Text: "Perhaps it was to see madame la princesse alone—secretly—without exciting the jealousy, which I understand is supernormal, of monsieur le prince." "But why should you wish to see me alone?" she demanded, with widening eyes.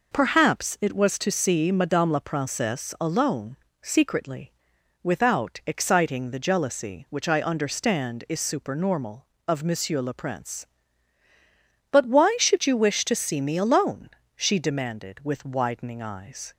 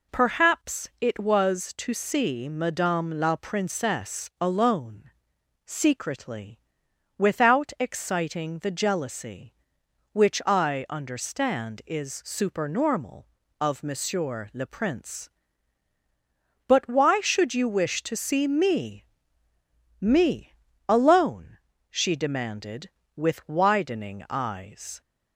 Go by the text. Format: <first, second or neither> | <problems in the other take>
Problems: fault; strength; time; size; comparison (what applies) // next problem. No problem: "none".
first | says "me" twice; at 19.9 s